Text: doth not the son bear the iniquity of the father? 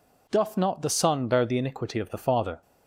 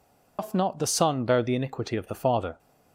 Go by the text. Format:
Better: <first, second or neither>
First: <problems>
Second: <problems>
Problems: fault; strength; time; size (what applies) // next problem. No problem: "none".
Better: first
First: none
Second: loses the start of "doth"; at 0.3 s; 125 ms